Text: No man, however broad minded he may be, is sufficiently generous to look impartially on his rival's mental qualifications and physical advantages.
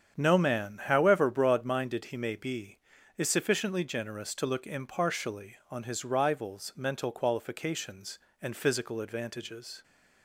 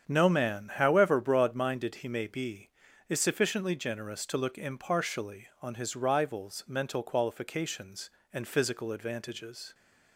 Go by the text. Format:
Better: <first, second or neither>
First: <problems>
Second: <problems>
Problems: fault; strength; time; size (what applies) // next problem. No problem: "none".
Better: neither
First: starts louder than the rest; strong; until 1.2 s; 8 dB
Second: starts louder than the rest; strong; until 1.1 s; 8 dB